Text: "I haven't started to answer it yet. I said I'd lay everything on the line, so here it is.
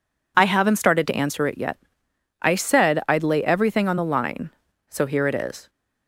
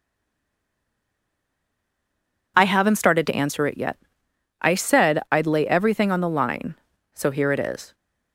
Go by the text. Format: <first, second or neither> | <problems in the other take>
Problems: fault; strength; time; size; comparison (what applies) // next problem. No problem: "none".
first | stays silent before the first word; strong; until 2.5 s; 2.5 s long